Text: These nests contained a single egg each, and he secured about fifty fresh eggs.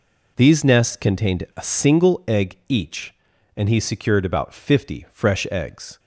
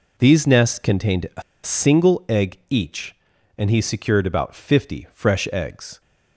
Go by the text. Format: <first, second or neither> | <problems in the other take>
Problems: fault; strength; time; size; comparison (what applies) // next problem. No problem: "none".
first | pauses between "a" and "single"; slight; at 1.4 s; 0.21 s long